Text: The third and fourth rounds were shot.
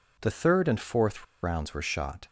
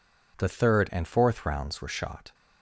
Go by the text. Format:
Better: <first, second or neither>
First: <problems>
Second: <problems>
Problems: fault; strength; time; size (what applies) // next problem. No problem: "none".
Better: second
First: pauses between "fourth" and "rounds"; slight; at 1.2 s; 0.19 s long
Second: none